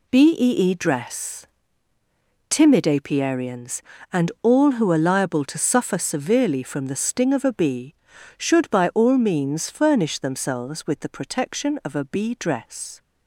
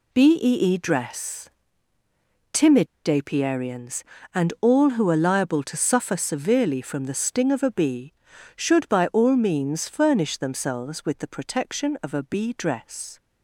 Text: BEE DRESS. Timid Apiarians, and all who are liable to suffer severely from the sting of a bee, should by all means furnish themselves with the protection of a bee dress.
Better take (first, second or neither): first